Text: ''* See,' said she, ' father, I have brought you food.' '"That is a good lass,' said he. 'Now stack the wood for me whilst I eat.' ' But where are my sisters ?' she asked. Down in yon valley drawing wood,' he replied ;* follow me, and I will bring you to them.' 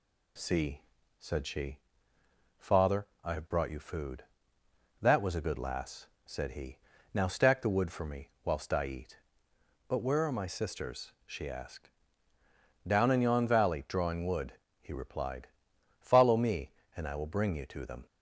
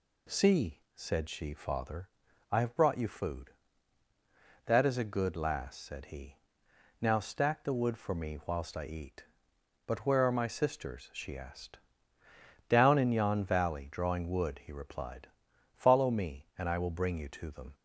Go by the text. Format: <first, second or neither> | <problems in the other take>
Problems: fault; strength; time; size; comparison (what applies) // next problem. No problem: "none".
second | says "was" for "is"; at 5.2 s // pauses between "me" and "whilst"; slight; at 8.2 s; 0.16 s long